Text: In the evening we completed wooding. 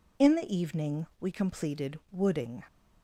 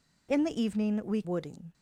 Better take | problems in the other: first | skips "completed"; at 1.2 s

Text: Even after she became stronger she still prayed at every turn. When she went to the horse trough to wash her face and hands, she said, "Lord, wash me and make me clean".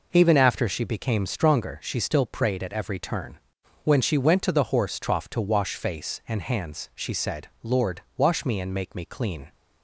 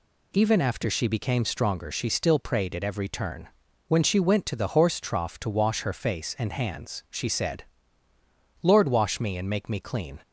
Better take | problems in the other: second | skips "her"; at 5.7 s

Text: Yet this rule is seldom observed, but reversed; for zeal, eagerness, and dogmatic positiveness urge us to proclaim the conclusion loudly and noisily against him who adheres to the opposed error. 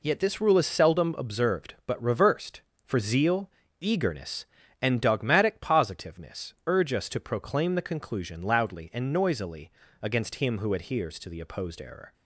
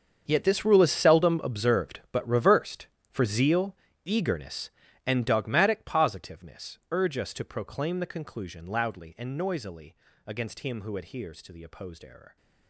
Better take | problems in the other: first | gets quieter; strong; throughout; 16 dB // pauses between "noisily" and "against"; slight; at 9.9 s; 0.32 s long; slight in the first

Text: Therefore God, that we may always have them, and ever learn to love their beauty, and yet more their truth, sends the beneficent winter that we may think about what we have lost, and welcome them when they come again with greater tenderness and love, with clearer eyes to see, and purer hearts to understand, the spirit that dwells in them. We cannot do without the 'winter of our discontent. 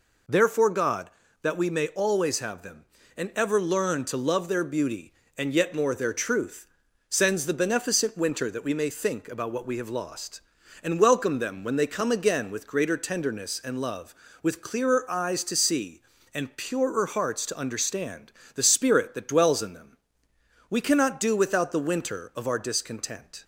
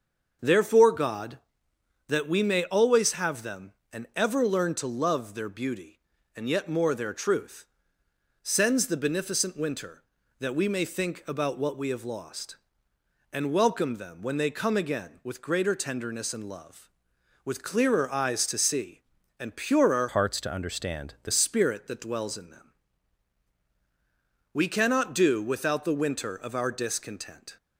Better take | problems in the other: first | starts louder than the rest; until 2.1 s; 6.5 dB // changes voice from "hearts" to "the"; from 20.0 to 21.3 s; 1.3 s long

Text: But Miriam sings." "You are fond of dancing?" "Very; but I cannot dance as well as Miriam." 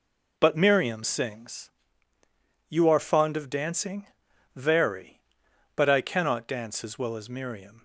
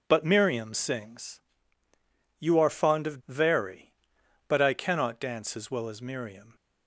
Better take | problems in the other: first | skips "dancing"; at 3.2 s

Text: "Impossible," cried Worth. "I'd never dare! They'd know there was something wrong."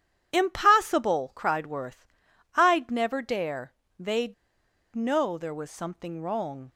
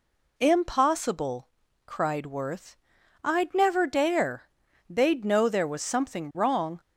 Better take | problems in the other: second | starts louder than the rest; strong; until 1.3 s; 9.5 dB // pauses between "They'd" and "know"; noticeable; at 4.3 s; 0.59 s long

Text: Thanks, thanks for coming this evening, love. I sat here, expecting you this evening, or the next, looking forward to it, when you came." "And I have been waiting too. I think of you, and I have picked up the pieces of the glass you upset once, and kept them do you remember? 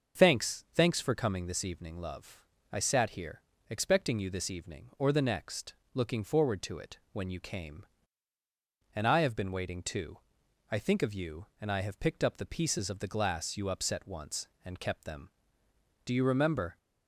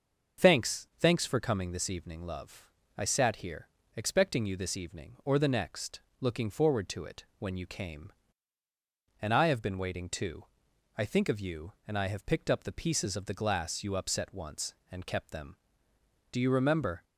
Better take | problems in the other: neither | starts louder than the rest; the same in both

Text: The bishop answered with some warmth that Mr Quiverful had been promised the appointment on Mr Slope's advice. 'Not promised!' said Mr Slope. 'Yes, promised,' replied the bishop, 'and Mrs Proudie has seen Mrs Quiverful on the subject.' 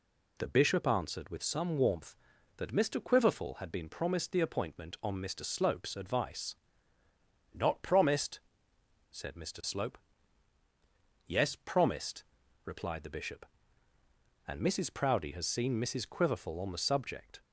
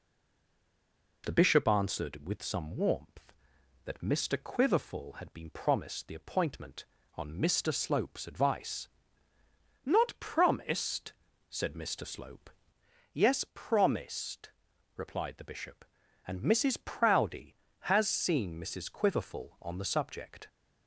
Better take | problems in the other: first | stays silent before the first word; noticeable; until 1.2 s; 1.2 s long

